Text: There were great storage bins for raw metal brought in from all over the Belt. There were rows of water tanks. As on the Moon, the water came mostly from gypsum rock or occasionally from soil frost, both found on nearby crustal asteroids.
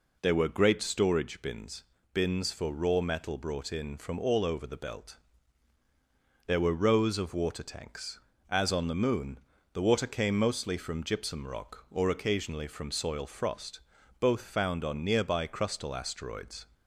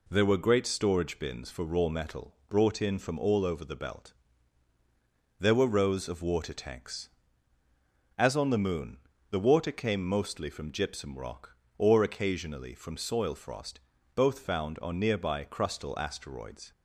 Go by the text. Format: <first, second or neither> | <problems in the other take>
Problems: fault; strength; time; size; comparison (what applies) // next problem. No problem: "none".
second | says "bins" twice; at 2.1 s